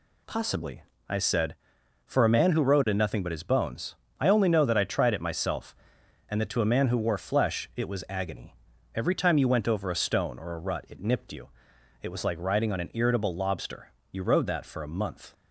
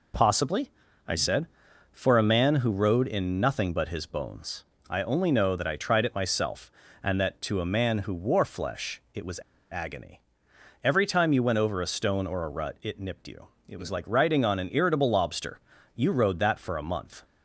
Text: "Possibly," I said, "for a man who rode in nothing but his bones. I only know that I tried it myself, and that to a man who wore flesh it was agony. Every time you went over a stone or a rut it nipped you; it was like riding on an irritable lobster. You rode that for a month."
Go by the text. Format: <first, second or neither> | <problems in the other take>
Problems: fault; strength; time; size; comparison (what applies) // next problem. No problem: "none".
first | pauses between "was" and "agony"; slight; at 9.4 s; 0.30 s long